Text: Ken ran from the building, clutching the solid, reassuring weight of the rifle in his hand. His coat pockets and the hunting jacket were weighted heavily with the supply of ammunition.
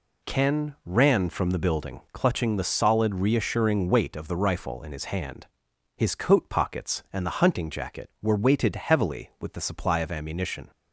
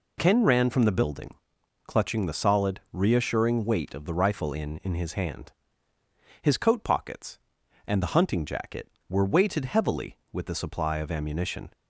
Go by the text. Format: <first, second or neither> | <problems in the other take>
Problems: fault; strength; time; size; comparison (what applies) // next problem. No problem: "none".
first | says "in" twice; at 4.8 s